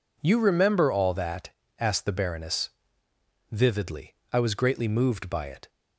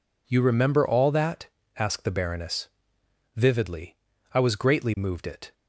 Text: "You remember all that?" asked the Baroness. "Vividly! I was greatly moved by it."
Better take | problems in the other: first | skips "by"; at 5.2 s

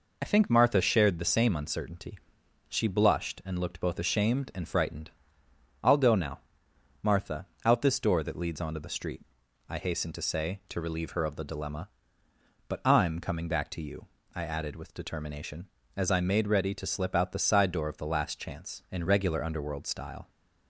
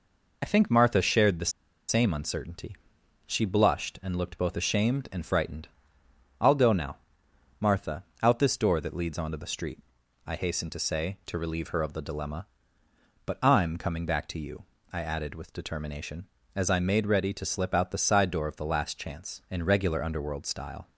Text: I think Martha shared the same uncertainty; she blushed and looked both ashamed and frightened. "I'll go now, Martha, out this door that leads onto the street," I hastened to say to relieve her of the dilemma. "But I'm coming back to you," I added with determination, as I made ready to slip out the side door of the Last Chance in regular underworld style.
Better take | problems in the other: first | pauses between "the" and "same"; at 1.5 s; 0.37 s long

